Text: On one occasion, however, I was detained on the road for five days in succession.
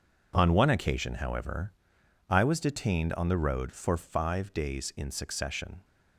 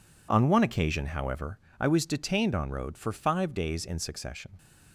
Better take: first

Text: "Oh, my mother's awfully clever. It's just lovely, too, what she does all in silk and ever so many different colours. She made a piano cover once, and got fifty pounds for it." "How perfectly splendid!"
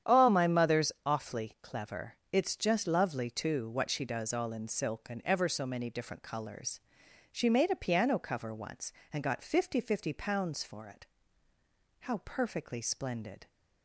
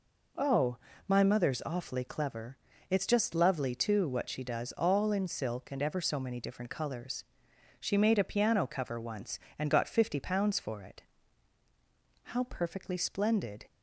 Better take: second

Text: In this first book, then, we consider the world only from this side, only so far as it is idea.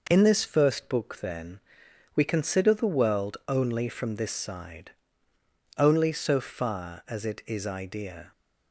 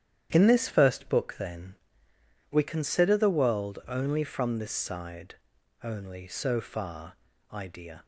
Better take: first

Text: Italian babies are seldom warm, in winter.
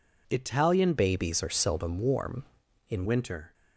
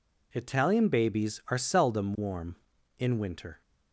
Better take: second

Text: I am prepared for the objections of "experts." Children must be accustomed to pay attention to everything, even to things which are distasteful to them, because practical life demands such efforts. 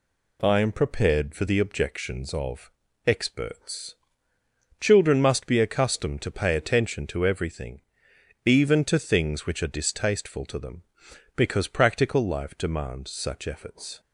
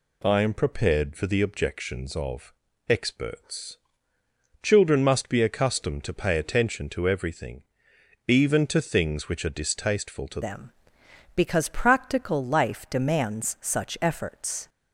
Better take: first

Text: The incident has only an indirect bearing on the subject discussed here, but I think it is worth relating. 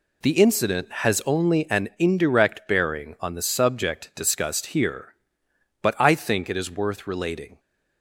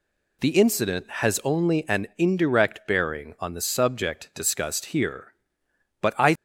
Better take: first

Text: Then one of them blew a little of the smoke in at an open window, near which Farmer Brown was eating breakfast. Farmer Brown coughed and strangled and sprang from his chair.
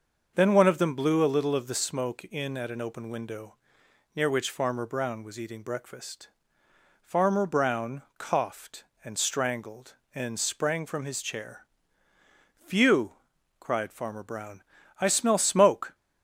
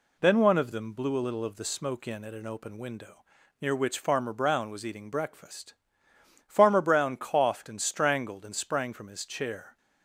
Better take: second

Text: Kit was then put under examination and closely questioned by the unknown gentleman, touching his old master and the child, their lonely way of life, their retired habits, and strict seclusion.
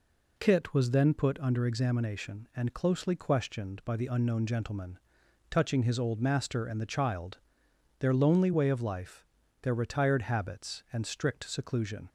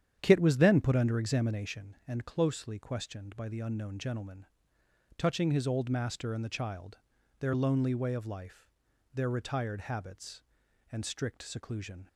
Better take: first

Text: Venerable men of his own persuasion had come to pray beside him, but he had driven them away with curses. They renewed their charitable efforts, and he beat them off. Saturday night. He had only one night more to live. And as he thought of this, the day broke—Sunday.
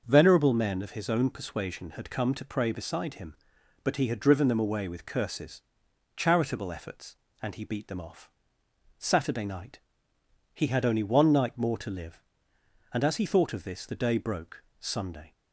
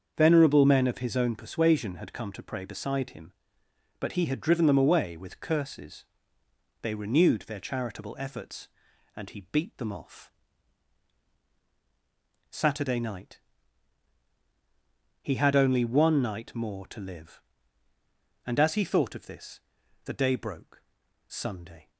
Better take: second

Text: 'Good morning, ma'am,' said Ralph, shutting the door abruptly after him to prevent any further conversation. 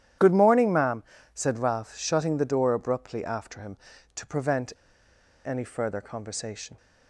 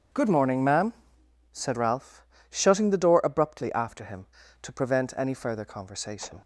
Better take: second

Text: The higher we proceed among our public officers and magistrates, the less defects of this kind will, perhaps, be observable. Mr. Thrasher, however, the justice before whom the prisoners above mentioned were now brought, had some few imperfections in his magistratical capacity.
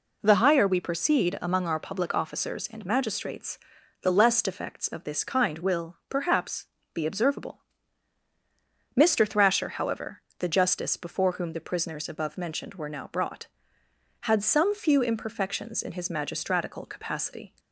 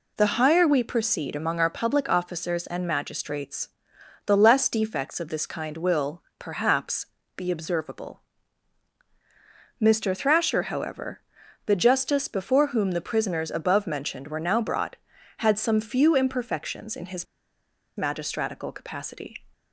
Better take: first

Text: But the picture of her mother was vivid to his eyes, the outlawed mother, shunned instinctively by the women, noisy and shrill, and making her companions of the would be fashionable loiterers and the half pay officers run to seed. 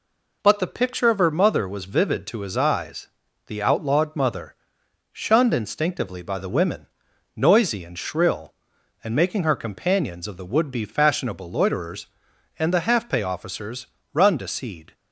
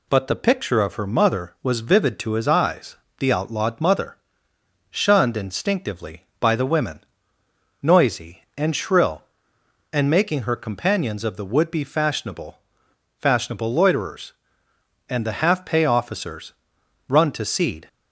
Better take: first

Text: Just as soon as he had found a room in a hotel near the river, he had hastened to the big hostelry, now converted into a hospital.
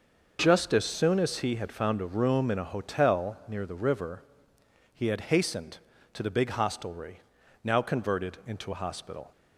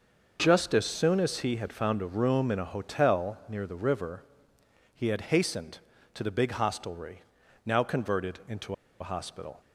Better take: first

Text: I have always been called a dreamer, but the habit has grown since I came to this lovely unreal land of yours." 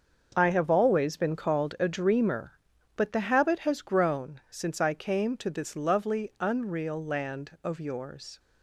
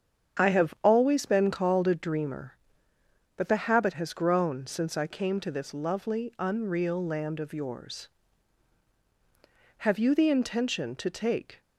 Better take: first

